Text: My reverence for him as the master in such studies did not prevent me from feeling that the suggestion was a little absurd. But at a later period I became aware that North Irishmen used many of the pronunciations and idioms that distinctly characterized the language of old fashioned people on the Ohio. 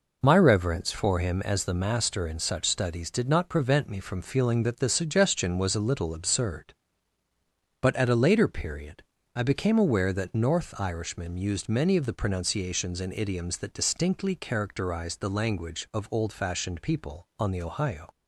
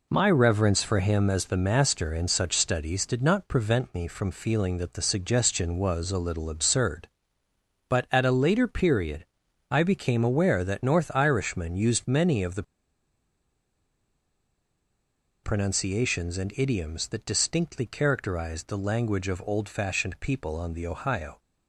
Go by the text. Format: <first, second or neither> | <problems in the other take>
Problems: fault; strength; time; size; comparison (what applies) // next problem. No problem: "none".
first | pauses between "period" and "I"; at 9.2 s; 0.42 s long; slight in the first // pauses between "the" and "pronunciations"; strong; at 12.6 s; 2.8 s long